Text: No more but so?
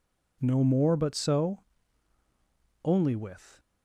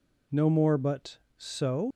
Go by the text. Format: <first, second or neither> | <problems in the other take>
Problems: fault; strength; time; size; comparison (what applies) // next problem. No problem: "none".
second | goes on to say "Only with"; noticeable; from 2.8 s on; 0.74 s long